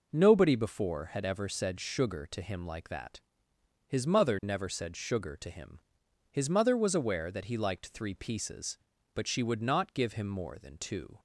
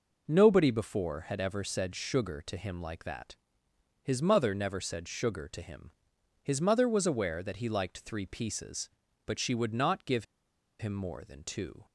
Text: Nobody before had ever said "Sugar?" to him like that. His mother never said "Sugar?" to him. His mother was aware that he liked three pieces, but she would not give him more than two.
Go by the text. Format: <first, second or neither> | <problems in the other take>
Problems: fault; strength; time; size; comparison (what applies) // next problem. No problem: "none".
first | pauses between "give" and "him"; noticeable; at 10.2 s; 0.54 s long